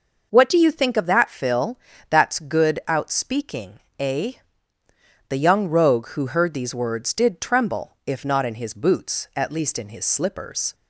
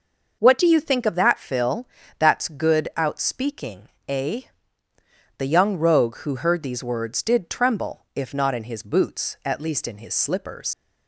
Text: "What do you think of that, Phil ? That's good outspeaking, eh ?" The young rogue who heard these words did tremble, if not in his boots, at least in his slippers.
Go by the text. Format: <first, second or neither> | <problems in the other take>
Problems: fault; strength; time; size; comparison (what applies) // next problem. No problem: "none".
first | leaves "slippers" unfinished; at 10.7 s; 105 ms